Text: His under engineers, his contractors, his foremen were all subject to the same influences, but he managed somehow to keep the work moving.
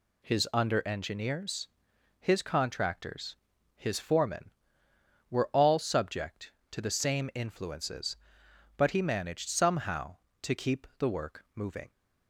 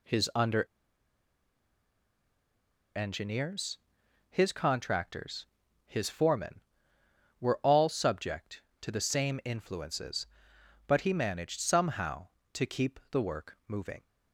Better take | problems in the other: first | pauses between "under" and "engineers"; strong; at 0.6 s; 2.2 s long

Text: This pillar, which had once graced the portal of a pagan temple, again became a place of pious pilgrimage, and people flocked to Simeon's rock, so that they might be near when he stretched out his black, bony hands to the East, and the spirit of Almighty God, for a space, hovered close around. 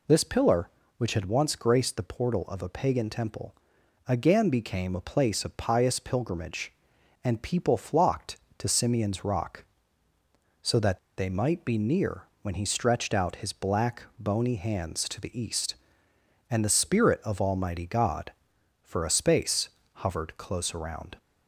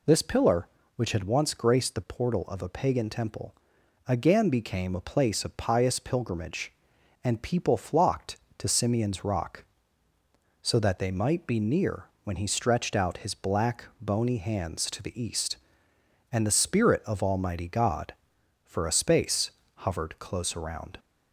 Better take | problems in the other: second | pauses between "that" and "they"; slight; at 10.9 s; 0.18 s long // pauses between "near" and "when"; slight; at 12.2 s; 0.18 s long; slight in the second

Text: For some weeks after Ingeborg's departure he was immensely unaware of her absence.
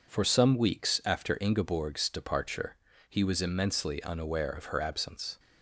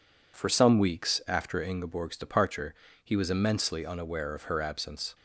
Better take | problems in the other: neither | pauses between "departure" and "he"; slight; the same in both

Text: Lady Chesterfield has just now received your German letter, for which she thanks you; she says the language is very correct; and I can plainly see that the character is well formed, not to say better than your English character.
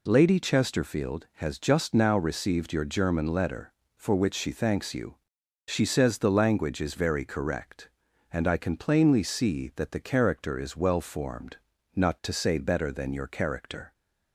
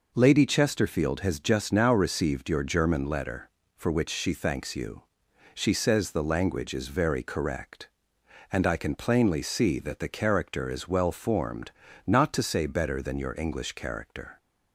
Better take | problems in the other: second | skips "English"; at 13.2 s

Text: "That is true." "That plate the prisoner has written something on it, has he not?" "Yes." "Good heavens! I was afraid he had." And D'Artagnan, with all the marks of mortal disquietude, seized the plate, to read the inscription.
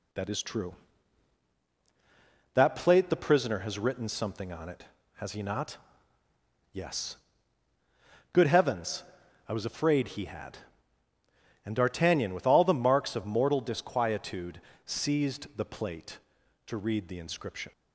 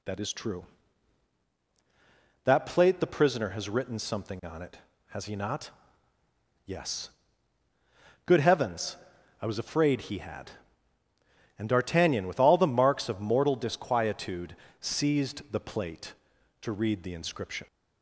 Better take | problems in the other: second | gets quieter; slight; throughout; 3.5 dB

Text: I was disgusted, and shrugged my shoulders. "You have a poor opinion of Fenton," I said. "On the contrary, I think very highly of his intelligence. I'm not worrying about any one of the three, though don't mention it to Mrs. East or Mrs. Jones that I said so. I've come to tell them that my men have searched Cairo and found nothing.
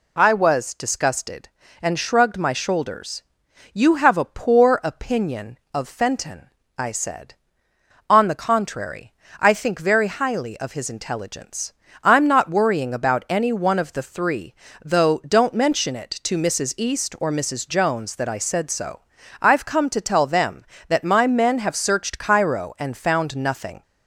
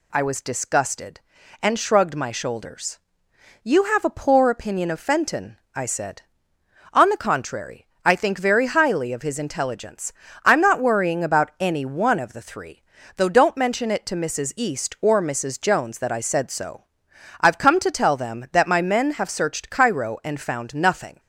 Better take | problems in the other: neither | none

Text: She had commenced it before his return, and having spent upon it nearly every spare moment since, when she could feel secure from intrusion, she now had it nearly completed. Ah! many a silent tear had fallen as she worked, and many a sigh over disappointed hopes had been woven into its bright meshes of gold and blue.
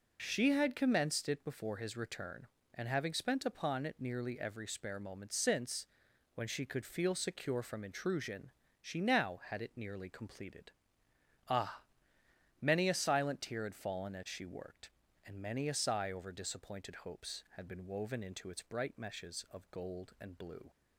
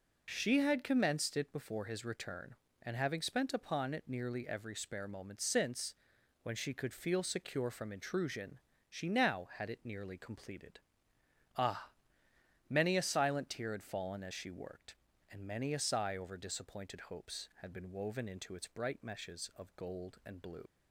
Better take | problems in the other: first | leaves "blue" unfinished; at 20.6 s; 80 ms

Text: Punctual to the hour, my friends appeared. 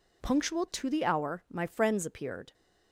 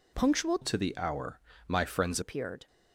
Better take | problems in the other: first | changes voice from "to" to "friends"; from 0.6 to 2.1 s; 1.5 s long

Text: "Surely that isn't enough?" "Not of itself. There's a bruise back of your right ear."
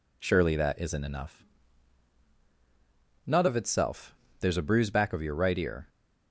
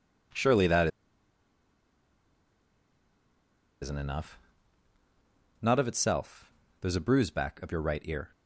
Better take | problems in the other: first | pauses between "that" and "isn't"; strong; at 0.8 s; 2.9 s long

